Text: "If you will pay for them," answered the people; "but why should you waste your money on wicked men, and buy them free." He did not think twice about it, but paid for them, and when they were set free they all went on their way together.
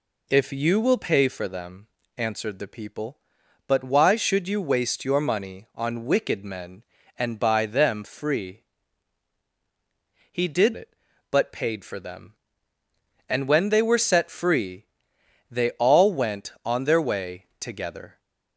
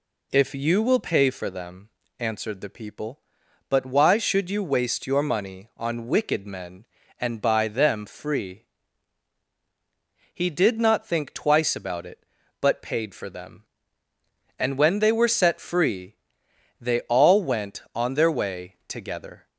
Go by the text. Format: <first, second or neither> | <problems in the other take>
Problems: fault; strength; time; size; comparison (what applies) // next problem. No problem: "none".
second | skips "not think twice about"; at 10.7 s // pauses between "free" and "they"; noticeable; at 14.8 s; 0.64 s long; noticeable in the second